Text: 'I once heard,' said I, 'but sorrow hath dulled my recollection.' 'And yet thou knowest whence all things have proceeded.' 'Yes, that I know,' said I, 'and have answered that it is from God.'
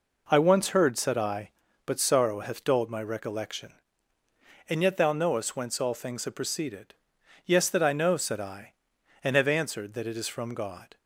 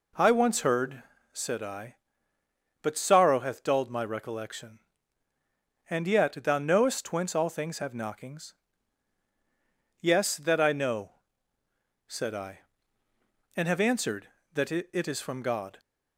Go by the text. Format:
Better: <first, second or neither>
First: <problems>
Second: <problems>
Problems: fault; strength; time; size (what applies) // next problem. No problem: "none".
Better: first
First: none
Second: says "knockings" for "proceeded"; at 7.9 s